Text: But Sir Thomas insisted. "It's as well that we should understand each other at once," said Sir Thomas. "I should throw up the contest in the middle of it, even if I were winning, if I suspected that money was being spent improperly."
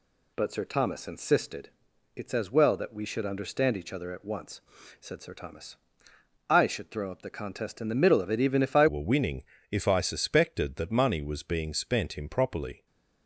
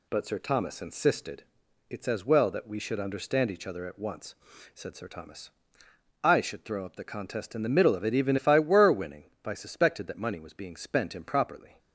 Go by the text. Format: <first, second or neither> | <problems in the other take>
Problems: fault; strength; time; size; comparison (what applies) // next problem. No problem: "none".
second | changes voice at "were"; from 8.8 s on; 4.0 s long